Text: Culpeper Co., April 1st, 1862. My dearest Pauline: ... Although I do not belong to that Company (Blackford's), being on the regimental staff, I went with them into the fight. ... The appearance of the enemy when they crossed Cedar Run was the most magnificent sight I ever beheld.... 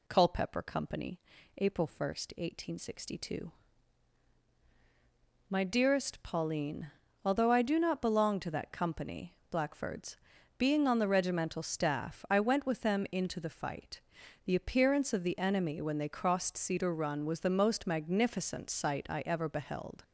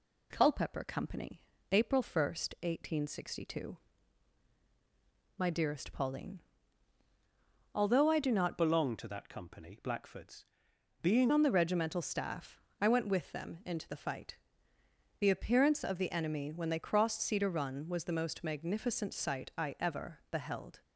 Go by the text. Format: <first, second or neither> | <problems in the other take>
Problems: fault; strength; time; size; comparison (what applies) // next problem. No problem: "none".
first | changes voice from "belong" to "being"; from 8.5 to 11.3 s; 2.8 s long